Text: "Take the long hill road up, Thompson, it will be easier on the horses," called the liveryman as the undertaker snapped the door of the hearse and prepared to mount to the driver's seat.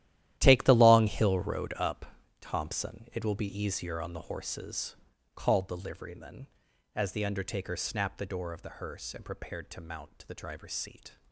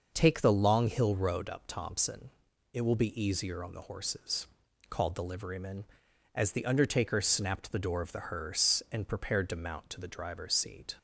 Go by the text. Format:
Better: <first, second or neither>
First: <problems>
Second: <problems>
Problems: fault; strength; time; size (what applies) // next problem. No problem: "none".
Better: second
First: gets quieter; strong; throughout; 14 dB // starts louder than the rest; strong; until 1.3 s; 12.5 dB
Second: starts louder than the rest; until 1.1 s; 6 dB